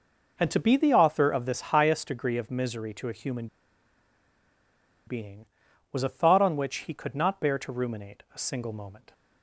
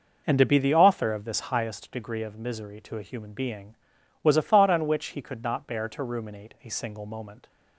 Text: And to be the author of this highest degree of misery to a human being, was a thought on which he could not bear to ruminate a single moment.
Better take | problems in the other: second | pauses between "human" and "being"; strong; at 3.4 s; 1.6 s long

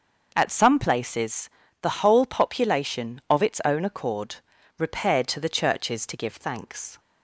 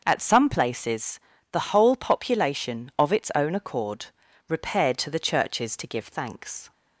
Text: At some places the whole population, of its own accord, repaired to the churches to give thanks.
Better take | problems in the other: neither | starts louder than the rest; the same in both // pauses between "places" and "the"; slight; the same in both

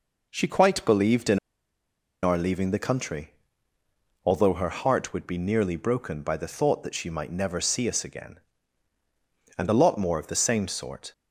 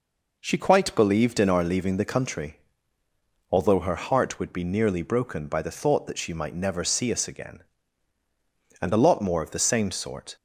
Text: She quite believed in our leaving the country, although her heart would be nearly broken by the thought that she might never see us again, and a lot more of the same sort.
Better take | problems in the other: second | pauses between "in" and "our"; noticeable; at 1.3 s; 0.84 s long

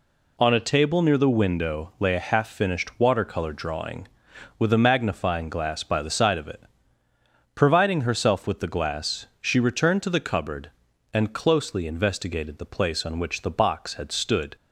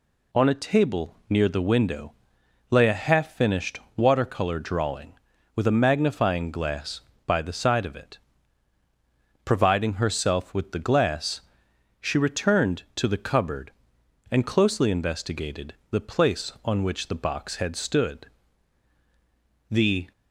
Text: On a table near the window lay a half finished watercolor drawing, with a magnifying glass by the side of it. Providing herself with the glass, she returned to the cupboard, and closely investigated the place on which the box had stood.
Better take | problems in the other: first | pauses between "window" and "lay"; noticeable; at 2.1 s; 0.56 s long // pauses between "finished" and "watercolor"; slight; at 3.7 s; 0.18 s long // pauses between "investigated" and "the"; slight; at 15.7 s; 0.16 s long // goes on to say "The"; slight; from 19.6 s on; 0.42 s long

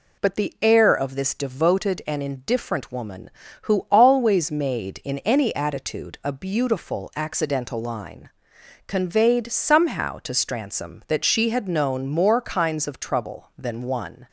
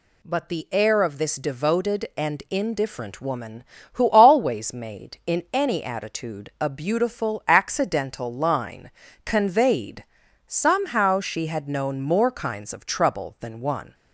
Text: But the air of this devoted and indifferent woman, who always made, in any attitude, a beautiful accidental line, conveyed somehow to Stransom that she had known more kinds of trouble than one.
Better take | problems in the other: first | pauses between "conveyed" and "somehow"; at 10.0 s; 0.42 s long // skips "to Stransom that"; at 11.1 s

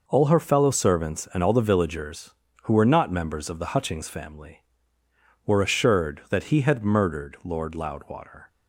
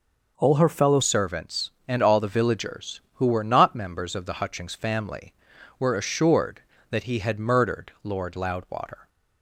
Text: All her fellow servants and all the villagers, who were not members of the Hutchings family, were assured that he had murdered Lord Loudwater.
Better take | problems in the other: first | changes voice at "servants"; from 1.0 s on; 8.0 s long

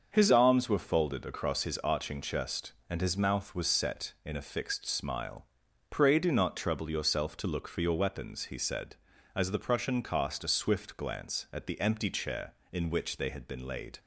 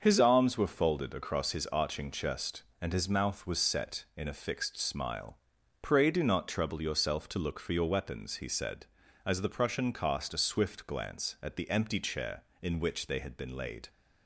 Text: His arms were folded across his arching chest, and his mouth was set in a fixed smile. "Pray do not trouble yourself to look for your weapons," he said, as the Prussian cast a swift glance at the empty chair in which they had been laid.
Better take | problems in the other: neither | starts louder than the rest; the same in both

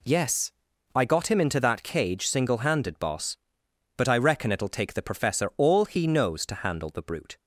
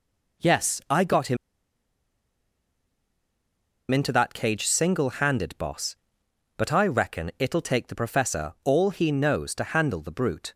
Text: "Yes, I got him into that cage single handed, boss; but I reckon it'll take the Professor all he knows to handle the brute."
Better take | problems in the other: first | pauses between "him" and "into"; strong; at 1.3 s; 2.5 s long

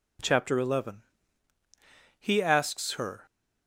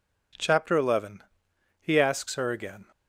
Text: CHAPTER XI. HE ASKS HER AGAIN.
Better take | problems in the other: second | stops before "AGAIN"; at 3.2 s

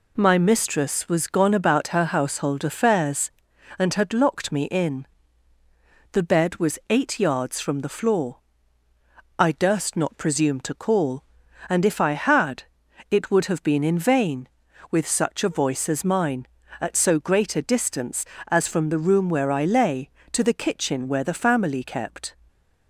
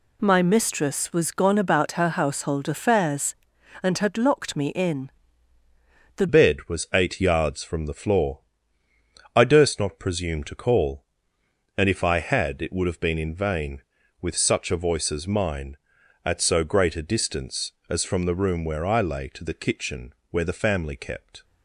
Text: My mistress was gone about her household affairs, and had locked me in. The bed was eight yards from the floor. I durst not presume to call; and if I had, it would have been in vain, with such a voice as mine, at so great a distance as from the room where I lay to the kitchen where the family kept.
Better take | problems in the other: first | changes voice at "bed"; from 6.2 s on; 15.2 s long // pauses between "kitchen" and "where"; slight; at 20.1 s; 0.18 s long

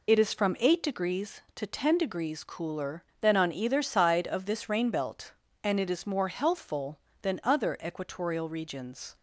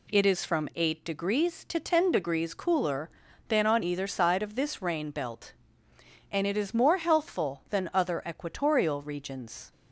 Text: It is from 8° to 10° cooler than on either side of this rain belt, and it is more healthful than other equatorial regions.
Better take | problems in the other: second | loses the start of "It"; at 0.0 s; 40 ms

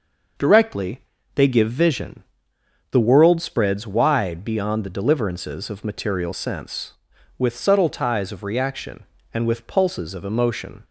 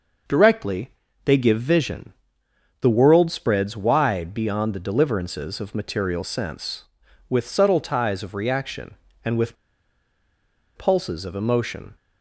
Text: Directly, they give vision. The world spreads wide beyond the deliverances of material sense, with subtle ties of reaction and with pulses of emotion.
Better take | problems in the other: first | pauses between "with" and "pulses"; at 9.5 s; 1.2 s long

